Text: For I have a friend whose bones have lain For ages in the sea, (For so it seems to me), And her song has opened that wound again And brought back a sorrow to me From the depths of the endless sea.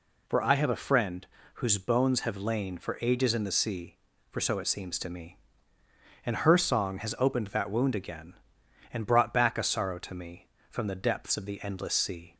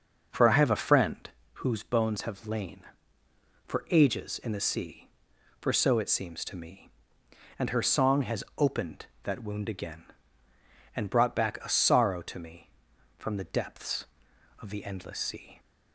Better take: first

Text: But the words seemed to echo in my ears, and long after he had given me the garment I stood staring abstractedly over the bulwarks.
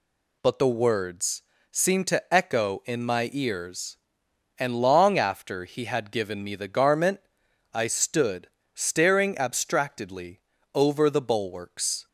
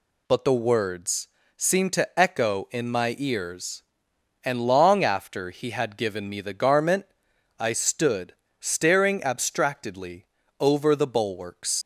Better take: first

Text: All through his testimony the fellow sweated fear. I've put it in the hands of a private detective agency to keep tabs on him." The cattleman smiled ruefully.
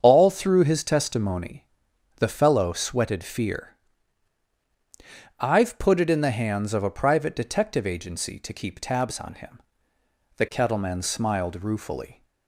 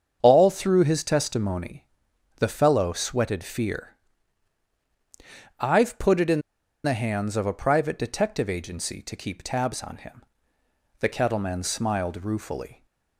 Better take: first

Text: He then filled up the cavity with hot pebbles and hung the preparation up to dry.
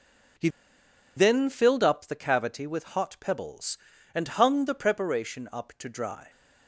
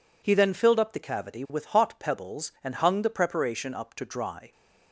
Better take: second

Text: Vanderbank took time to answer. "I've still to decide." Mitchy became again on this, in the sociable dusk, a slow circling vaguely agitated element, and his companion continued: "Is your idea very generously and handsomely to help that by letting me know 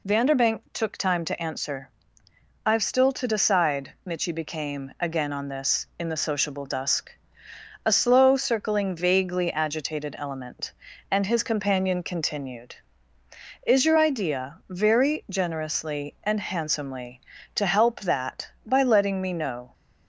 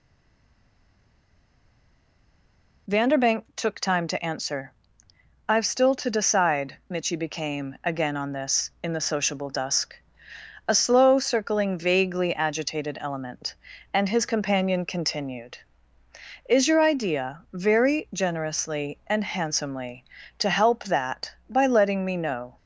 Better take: first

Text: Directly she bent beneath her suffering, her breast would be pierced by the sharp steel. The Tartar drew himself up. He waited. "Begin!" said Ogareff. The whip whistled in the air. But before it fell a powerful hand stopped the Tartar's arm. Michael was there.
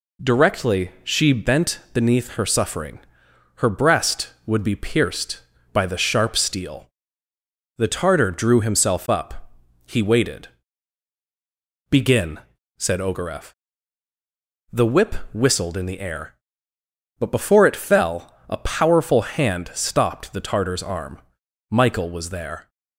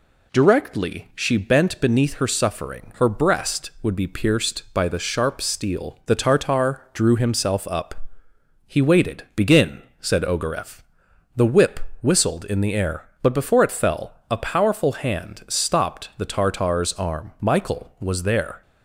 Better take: neither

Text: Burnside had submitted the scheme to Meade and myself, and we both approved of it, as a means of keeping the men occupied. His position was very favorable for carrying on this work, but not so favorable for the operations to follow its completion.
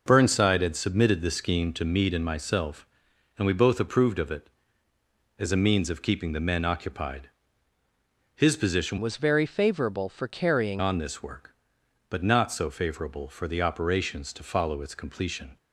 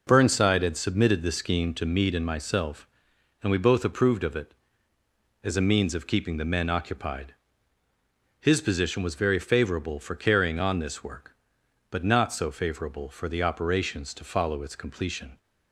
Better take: second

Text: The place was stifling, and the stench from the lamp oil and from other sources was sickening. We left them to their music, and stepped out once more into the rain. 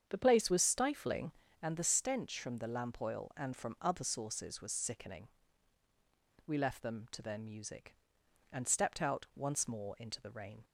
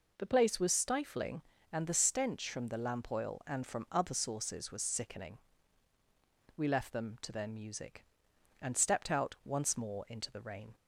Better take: second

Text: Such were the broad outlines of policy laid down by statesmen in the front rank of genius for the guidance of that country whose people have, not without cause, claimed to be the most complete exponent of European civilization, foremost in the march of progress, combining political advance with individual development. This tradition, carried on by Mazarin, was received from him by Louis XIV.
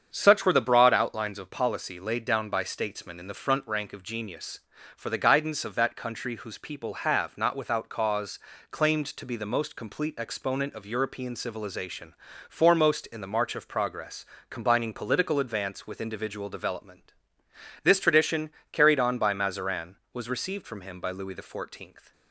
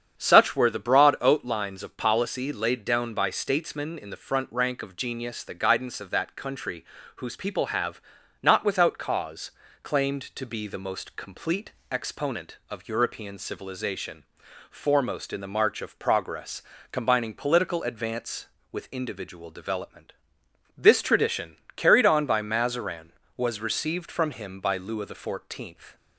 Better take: first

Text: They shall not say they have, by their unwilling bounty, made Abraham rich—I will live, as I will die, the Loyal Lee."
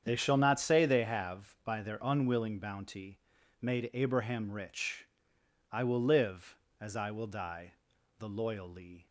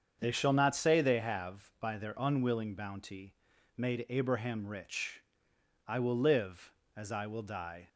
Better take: first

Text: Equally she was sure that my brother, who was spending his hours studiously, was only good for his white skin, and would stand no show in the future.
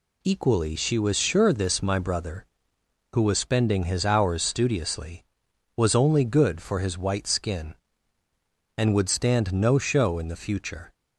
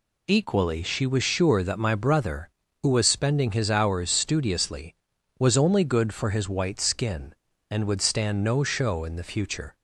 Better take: second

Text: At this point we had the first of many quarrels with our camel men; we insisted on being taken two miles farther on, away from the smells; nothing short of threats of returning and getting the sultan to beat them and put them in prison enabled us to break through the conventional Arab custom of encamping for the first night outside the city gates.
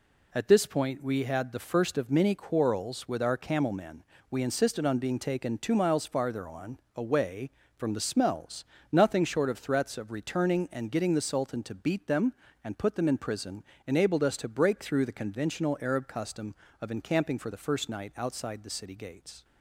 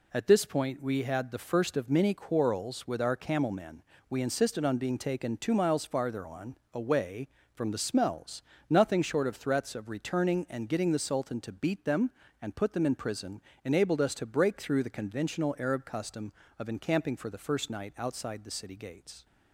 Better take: neither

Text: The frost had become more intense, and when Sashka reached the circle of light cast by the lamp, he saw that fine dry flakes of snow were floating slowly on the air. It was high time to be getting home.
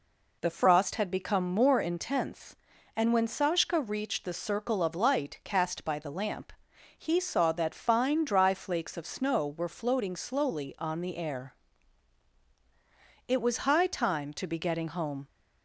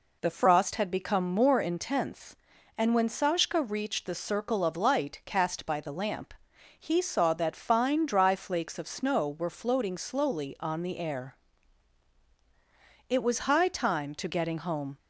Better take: first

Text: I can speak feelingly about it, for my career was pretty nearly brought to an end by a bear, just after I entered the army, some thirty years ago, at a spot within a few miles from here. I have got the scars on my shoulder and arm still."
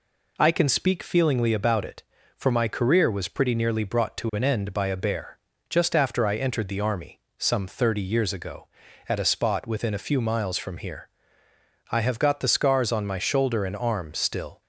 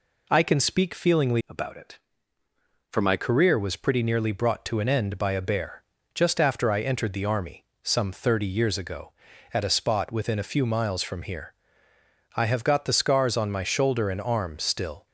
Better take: first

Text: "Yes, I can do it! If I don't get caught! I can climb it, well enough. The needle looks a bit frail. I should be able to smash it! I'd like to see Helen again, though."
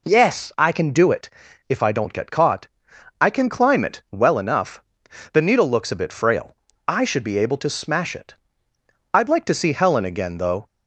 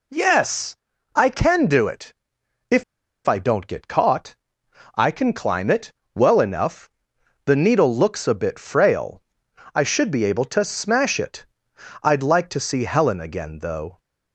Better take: first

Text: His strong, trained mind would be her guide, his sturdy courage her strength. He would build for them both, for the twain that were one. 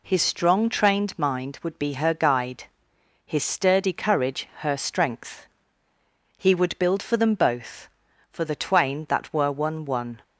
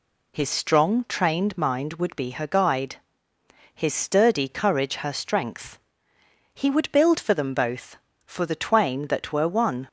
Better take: second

